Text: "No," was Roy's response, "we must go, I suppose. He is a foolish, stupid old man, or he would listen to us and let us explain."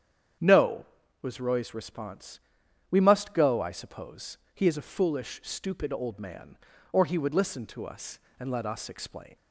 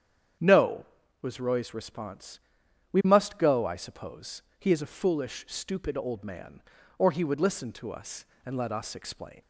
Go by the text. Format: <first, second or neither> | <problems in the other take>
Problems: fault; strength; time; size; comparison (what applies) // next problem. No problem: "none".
neither | starts louder than the rest; strong; the same in both